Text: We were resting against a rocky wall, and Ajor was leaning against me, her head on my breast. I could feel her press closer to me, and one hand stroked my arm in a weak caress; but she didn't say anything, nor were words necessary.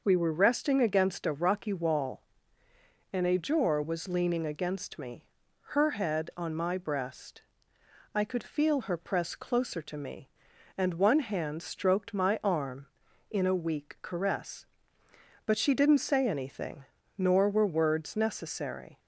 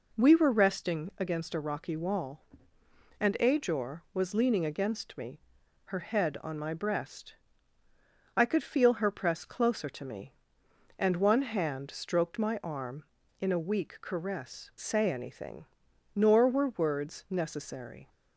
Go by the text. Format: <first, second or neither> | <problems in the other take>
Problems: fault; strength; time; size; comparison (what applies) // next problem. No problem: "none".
first | skips "but she didn't"; at 14.7 s